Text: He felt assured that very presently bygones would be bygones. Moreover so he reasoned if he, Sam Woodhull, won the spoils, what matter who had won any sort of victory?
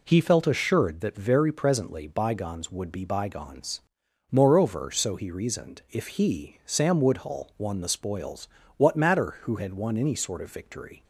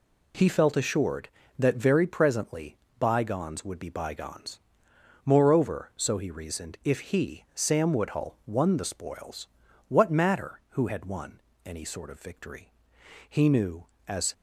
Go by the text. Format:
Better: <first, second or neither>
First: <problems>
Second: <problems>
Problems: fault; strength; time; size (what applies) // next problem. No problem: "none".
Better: first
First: none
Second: pauses between "presently" and "bygones"; slight; at 2.7 s; 0.24 s long // pauses between "won" and "any"; slight; at 11.3 s; 0.28 s long // goes on to say "He knew as"; noticeable; from 13.2 s on; 1.0 s long